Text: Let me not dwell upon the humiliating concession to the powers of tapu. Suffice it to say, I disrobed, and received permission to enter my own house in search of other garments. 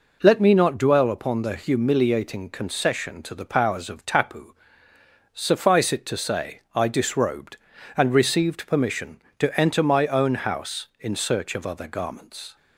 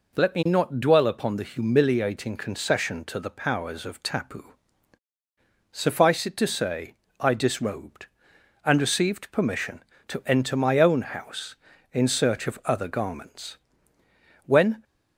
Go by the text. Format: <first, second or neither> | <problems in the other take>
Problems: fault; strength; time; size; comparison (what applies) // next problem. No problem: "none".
first | goes on to say "When"; slight; from 14.4 s on; 0.38 s long